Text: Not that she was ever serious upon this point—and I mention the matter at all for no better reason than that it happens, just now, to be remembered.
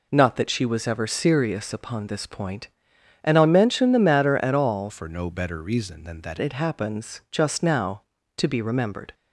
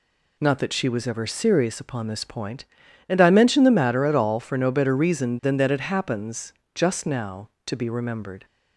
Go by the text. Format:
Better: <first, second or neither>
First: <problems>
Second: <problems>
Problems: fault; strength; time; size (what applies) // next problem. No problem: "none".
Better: second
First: changes voice from "for" to "that"; from 4.8 to 6.3 s; 1.5 s long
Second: none